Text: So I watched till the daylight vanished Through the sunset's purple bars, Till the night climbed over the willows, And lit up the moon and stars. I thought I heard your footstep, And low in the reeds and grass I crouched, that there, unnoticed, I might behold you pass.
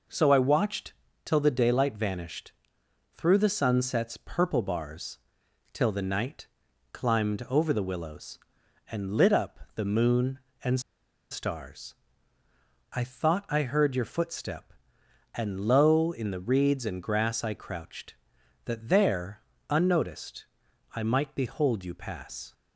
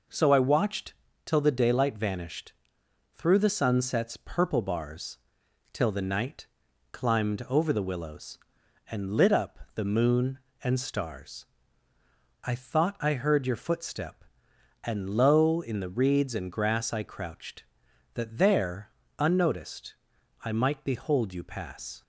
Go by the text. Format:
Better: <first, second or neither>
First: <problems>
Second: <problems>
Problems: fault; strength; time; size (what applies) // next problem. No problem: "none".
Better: second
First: pauses between "watched" and "till"; slight; at 0.9 s; 0.30 s long // pauses between "vanished" and "Through"; noticeable; at 2.5 s; 0.60 s long // pauses between "night" and "climbed"; noticeable; at 6.4 s; 0.46 s long // pauses between "up" and "the"; slight; at 9.5 s; 0.16 s long // pauses between "and" and "stars"; noticeable; at 10.8 s; 0.50 s long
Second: pauses between "watched" and "till"; slight; at 0.9 s; 0.30 s long // pauses between "vanished" and "Through"; noticeable; at 2.5 s; 0.60 s long // pauses between "night" and "climbed"; noticeable; at 6.4 s; 0.46 s long // pauses between "up" and "the"; slight; at 9.5 s; 0.16 s long